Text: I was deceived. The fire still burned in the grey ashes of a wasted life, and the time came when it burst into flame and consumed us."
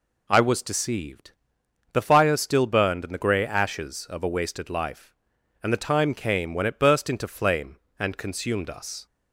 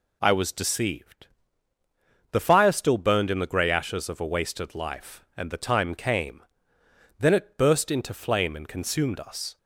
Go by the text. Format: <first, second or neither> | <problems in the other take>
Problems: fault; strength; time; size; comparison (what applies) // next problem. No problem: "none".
first | says "then" for "when"; at 7.2 s